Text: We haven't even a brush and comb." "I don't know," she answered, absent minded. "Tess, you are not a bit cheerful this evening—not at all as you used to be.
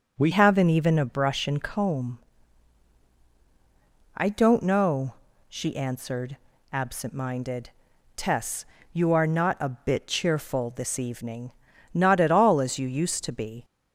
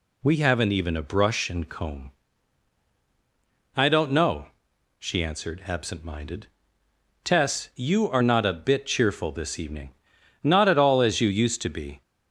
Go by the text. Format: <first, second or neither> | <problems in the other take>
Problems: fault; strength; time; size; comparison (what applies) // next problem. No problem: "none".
second | starts louder than the rest; until 1.1 s; 6.5 dB // changes voice at "haven't"; from 0.3 s on; 13.3 s long